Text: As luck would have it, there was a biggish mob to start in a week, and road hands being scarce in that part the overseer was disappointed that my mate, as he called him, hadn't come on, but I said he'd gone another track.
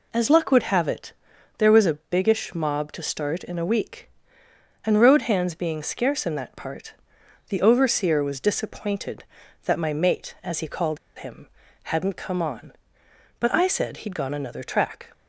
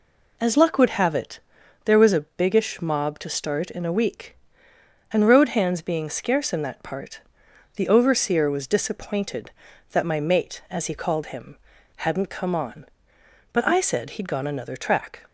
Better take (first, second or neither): second